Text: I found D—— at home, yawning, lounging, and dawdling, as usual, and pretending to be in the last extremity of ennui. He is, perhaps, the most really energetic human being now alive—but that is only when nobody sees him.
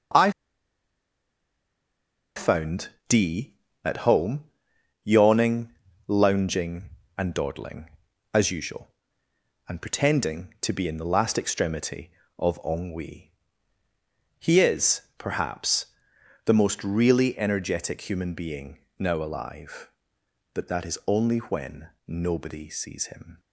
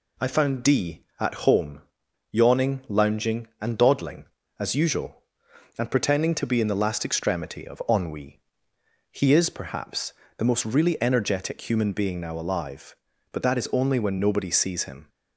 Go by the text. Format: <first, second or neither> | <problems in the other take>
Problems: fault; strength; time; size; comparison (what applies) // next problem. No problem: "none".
second | pauses between "I" and "found"; strong; at 0.3 s; 2.0 s long // pauses between "found" and "D"; slight; at 2.8 s; 0.22 s long // pauses between "being" and "now"; slight; at 18.7 s; 0.20 s long // pauses between "when" and "nobody"; slight; at 21.8 s; 0.20 s long